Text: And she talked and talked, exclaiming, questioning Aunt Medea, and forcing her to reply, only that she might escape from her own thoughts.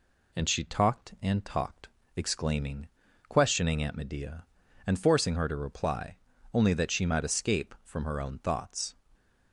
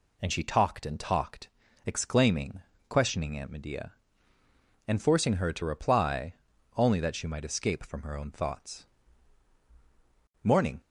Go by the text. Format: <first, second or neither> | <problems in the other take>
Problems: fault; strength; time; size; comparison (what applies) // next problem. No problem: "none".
first | goes on to say "Morning"; slight; from 10.4 s on; 0.38 s long